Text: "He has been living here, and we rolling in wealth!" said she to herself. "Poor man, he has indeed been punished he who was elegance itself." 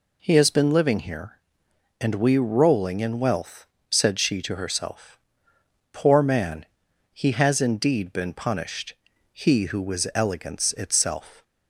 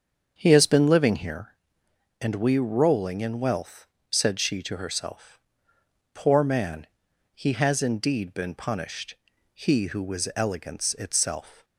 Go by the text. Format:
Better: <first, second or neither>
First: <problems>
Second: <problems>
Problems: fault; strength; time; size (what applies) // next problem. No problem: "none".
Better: first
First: pauses between "punished" and "he"; slight; at 8.9 s; 0.36 s long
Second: starts louder than the rest; until 1.6 s; 7 dB // pauses between "punished" and "he"; slight; at 9.1 s; 0.36 s long